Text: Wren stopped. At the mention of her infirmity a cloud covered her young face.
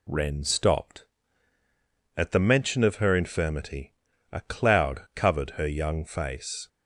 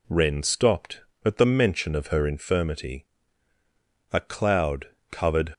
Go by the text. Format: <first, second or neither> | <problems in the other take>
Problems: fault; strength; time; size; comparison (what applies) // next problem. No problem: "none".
first | pauses between "infirmity" and "a"; at 3.0 s; 1.0 s long; also in the first // pauses between "cloud" and "covered"; slight; at 4.8 s; 0.24 s long // stops before "her young face"; at 5.5 s